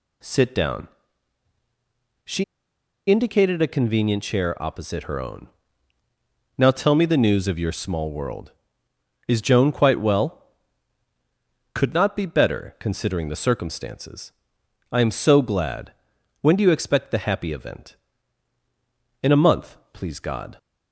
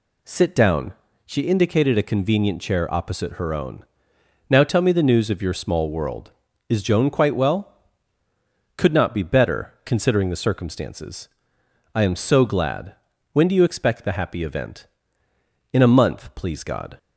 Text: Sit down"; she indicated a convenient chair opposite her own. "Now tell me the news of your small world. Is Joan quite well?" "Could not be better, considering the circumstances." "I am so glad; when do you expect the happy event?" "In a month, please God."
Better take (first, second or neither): second